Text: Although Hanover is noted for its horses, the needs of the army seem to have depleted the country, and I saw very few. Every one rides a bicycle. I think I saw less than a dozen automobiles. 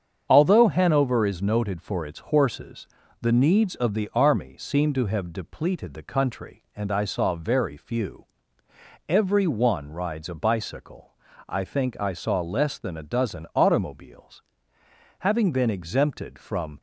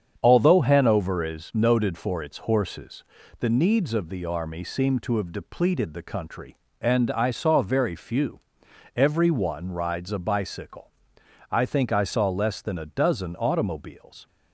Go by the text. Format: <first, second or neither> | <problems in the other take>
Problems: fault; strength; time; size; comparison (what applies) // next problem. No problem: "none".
second | starts louder than the rest; strong; until 1.3 s; 7.5 dB; strong in the second // goes on to say "Having been exempted from"; from 15.2 s on; 1.5 s long